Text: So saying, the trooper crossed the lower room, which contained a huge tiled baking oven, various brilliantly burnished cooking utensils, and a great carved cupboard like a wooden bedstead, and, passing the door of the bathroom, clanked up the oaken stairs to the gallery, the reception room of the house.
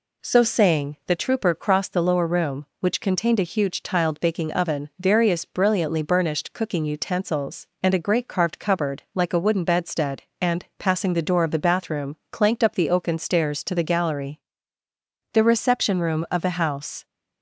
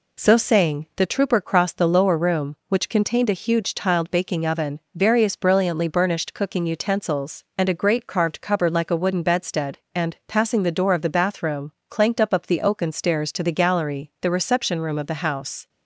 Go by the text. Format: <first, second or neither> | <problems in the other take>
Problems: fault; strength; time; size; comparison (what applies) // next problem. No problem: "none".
first | says "up" twice; at 12.3 s